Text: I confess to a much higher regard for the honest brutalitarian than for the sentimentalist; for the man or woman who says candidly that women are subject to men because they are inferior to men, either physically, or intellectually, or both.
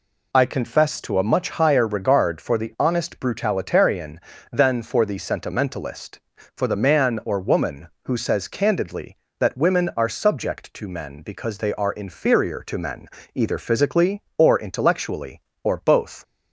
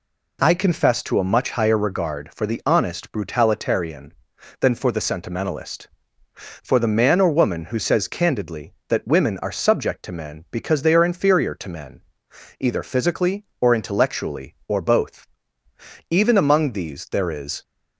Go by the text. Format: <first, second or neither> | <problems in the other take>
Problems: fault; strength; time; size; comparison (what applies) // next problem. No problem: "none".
first | goes on to say "Even among these there is"; from 16.0 s on; 1.5 s long